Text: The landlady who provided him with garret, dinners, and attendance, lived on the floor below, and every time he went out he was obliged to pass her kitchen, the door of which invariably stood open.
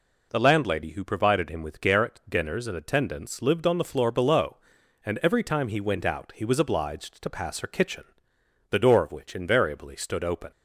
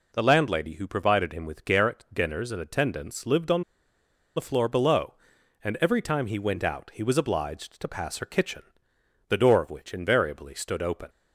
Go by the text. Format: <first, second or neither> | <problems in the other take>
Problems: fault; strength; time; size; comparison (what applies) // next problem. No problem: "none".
first | pauses between "on" and "the"; noticeable; at 3.6 s; 0.73 s long